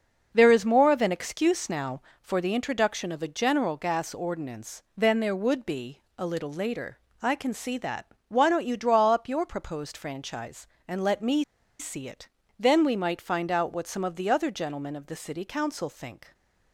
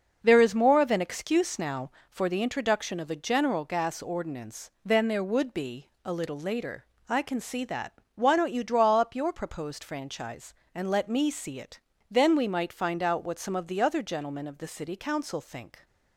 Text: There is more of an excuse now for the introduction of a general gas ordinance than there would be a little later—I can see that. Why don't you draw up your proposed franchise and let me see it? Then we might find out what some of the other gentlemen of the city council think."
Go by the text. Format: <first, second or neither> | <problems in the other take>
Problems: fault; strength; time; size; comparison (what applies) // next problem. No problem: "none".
second | starts louder than the rest; until 1.3 s; 6 dB; also in the second // pauses between "be" and "a"; slight; at 6.0 s; 0.16 s long // pauses between "me" and "see"; slight; at 11.4 s; 0.35 s long